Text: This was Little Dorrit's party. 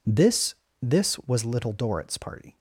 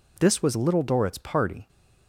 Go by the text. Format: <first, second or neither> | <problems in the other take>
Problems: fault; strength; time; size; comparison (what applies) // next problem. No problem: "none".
second | says "This" twice; at 0.8 s